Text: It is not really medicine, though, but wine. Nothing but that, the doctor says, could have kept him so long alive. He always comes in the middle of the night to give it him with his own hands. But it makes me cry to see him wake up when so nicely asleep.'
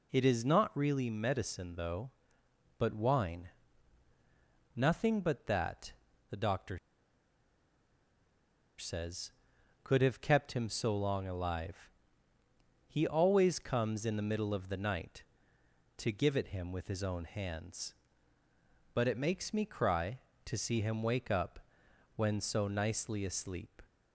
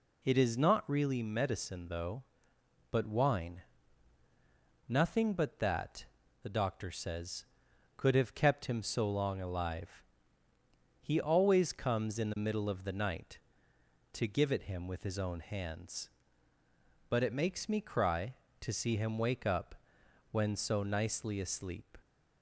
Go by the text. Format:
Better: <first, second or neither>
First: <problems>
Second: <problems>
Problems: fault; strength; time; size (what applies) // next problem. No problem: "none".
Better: second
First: pauses between "doctor" and "says"; strong; at 6.7 s; 1.9 s long // pauses between "up" and "when"; noticeable; at 21.5 s; 0.56 s long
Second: pauses between "up" and "when"; noticeable; at 19.7 s; 0.56 s long